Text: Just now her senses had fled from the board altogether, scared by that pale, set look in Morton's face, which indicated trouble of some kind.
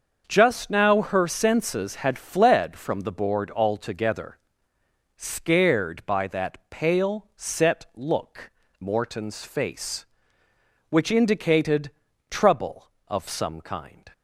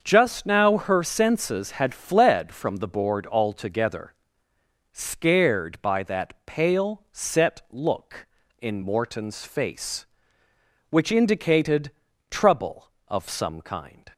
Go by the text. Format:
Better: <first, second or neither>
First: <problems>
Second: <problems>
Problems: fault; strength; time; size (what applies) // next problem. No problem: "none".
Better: second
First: starts louder than the rest; until 1.2 s; 6.5 dB // skips "in"; at 8.6 s // pauses between "indicated" and "trouble"; at 11.9 s; 0.40 s long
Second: starts louder than the rest; until 1.0 s; 6.5 dB // pauses between "indicated" and "trouble"; at 11.9 s; 0.40 s long